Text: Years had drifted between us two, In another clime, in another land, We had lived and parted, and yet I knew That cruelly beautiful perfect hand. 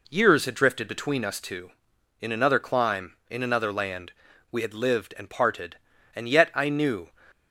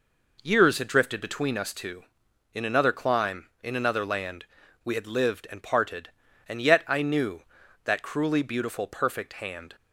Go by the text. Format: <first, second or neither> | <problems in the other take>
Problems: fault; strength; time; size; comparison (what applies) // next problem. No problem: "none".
second | stops before "That cruelly beautiful perfect hand"; at 7.3 s